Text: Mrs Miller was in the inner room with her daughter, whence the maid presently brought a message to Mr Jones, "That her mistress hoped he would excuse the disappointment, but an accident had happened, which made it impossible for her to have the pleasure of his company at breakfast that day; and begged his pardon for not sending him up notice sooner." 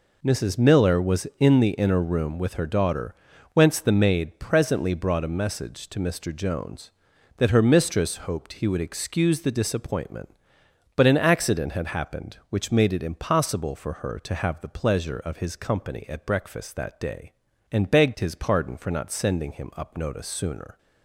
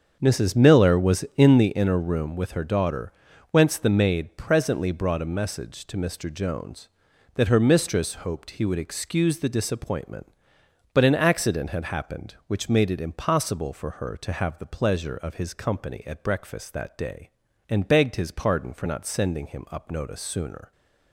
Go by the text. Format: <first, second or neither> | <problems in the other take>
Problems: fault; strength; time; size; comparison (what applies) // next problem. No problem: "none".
first | starts louder than the rest; until 1.8 s; 7 dB